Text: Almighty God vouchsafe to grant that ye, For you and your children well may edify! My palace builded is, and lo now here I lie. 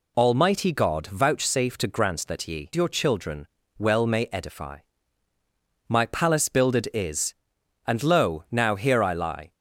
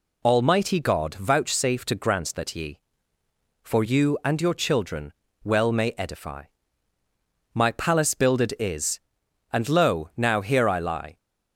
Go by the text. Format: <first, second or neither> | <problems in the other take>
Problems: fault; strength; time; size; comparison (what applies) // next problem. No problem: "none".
second | skips "For you and"; at 2.7 s // pauses between "children" and "well"; slight; at 3.4 s; 0.30 s long; slight in the second